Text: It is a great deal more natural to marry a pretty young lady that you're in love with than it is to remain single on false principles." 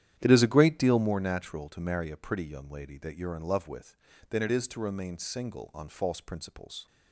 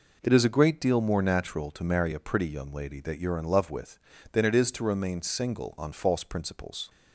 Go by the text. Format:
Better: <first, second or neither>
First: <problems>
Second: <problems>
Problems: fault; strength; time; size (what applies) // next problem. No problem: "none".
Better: second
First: starts louder than the rest; strong; until 1.1 s; 10.5 dB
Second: none